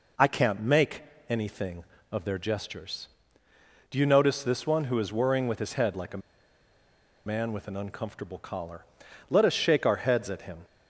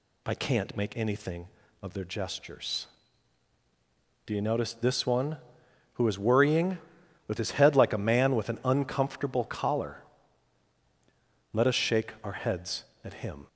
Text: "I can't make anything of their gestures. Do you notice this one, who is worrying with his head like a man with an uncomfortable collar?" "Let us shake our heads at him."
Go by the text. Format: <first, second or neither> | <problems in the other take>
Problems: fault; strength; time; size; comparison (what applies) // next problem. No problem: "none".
second | pauses between "make" and "anything"; slight; at 1.0 s; 0.26 s long // pauses between "a" and "man"; at 6.2 s; 1.0 s long